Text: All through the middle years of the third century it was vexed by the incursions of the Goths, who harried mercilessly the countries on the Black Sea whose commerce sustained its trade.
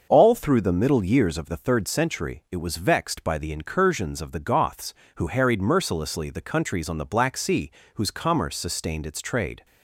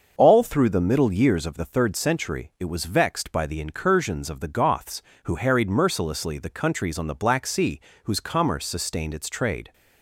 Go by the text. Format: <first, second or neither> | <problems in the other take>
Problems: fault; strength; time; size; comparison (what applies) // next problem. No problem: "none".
neither | starts louder than the rest; the same in both // pauses between "Sea" and "whose"; slight; the same in both